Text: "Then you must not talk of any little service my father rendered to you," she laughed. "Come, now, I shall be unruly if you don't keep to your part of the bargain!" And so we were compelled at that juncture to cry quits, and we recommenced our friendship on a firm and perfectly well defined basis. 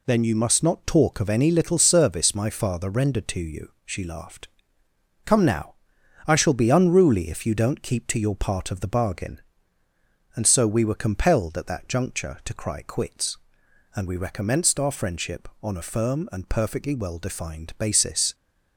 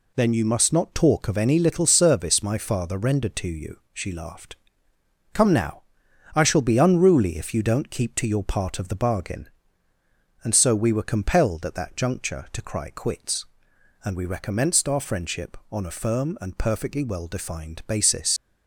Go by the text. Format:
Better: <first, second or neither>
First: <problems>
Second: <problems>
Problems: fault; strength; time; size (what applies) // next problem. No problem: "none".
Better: first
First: none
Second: leaves "basis" unfinished; at 18.3 s; 70 ms